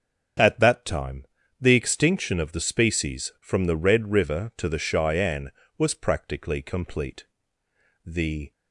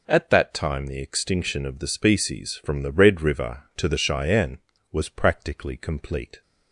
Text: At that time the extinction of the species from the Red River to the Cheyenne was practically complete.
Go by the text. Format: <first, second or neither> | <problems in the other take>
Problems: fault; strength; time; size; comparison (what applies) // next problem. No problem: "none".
second | starts louder than the rest; until 1.7 s; 7 dB // pauses between "time" and "the"; slight; at 1.2 s; 0.36 s long // goes on to say "The"; slight; from 8.0 s on; 0.48 s long